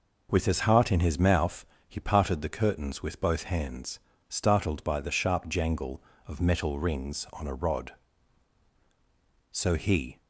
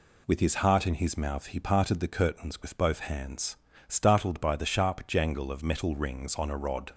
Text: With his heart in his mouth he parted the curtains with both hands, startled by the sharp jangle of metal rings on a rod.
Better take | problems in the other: second | pauses between "mouth" and "he"; slight; at 1.6 s; 0.24 s long // goes on to say "So he"; noticeable; from 9.5 s on; 0.70 s long

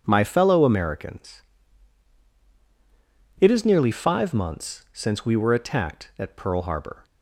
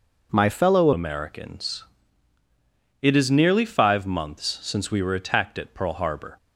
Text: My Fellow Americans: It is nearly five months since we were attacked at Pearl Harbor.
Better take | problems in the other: first | changes voice at "Americans"; from 0.9 s on; 5.4 s long

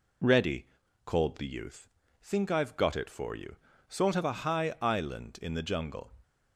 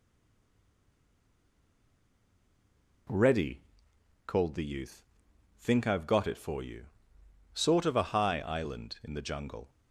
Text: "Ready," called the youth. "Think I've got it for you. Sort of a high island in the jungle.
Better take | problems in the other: first | stays silent before the first word; strong; until 3.0 s; 3.0 s long

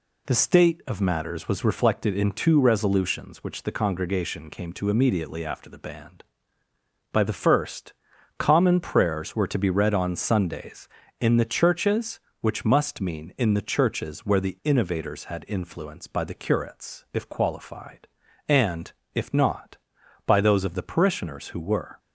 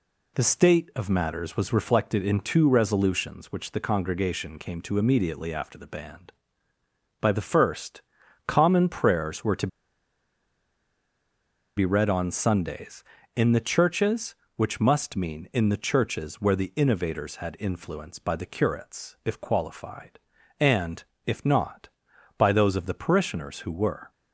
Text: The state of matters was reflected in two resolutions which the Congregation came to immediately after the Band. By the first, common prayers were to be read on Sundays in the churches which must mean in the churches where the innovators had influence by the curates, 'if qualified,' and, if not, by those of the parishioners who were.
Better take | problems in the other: first | pauses between "to" and "be"; strong; at 9.6 s; 2.0 s long

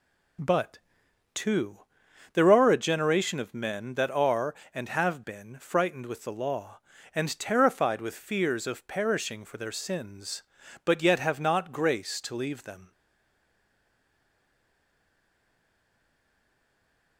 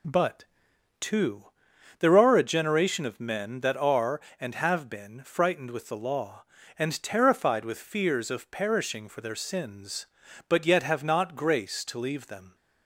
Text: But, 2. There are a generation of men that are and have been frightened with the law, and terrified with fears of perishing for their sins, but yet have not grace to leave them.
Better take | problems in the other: second | stays silent after the last word; strong; from 12.9 s on; 4.2 s long

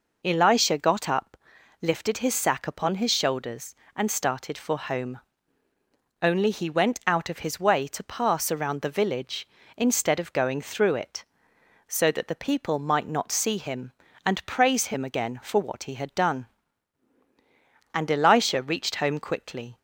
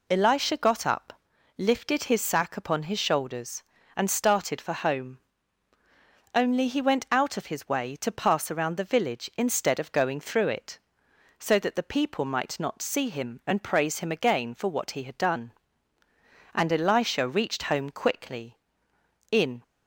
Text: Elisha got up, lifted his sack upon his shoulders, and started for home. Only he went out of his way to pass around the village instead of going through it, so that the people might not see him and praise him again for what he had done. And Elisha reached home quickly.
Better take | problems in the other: first | goes on to say "In"; slight; from 19.3 s on; 0.32 s long

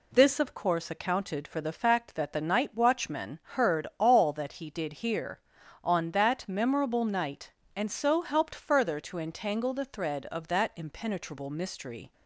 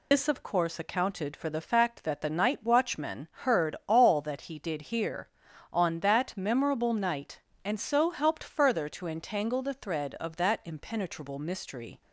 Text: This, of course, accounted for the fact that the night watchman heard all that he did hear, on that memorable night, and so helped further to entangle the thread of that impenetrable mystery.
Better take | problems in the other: first | loses the start of "This"; at 0.1 s; 105 ms // pauses between "watchman" and "heard"; slight; at 3.2 s; 0.16 s long; slight in the first

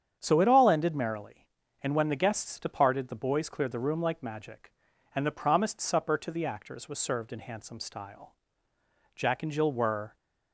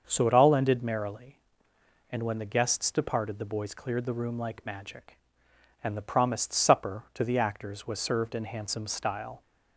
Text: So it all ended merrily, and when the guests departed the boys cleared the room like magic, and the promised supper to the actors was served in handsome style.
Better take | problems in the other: second | starts louder than the rest; strong; until 1.2 s; 8.5 dB; also in the second // goes on to say "Jack and Jill were"; noticeable; from 9.1 s on; 1.0 s long

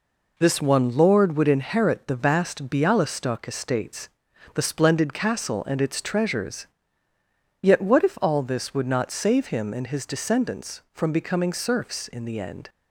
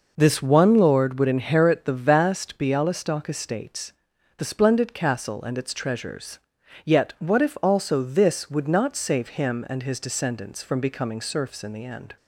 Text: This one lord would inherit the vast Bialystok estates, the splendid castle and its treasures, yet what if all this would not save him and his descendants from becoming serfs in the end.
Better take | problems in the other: first | says "also" for "all"; at 7.6 s

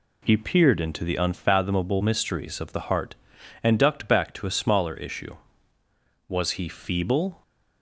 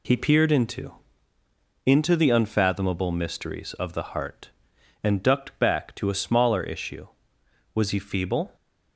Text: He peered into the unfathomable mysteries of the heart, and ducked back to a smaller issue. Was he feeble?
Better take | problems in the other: first | says "into" twice; at 1.8 s

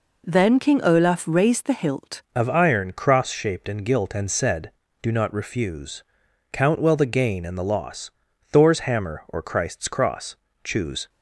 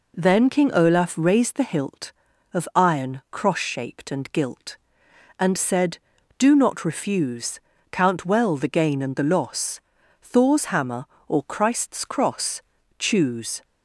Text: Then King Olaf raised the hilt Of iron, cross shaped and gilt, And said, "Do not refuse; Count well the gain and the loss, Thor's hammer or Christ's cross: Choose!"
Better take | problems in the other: second | changes voice at "Of"; from 2.3 s on; 8.7 s long

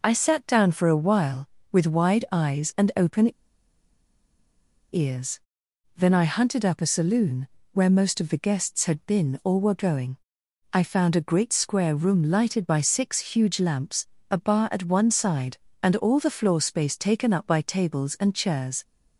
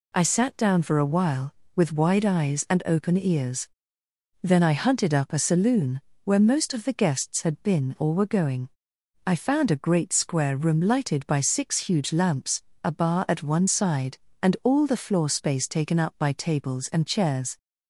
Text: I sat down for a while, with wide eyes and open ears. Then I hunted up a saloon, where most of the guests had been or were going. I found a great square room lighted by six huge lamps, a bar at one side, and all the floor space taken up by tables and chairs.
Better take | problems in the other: second | pauses between "open" and "ears"; strong; at 3.3 s; 1.6 s long

